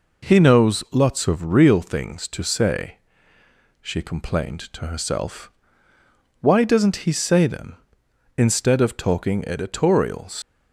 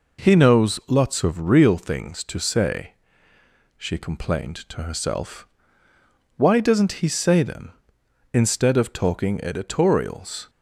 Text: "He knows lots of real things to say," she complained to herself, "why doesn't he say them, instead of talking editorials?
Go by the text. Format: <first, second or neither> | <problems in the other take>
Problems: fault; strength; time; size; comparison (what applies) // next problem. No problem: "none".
second | leaves "editorials" unfinished; at 10.4 s; 115 ms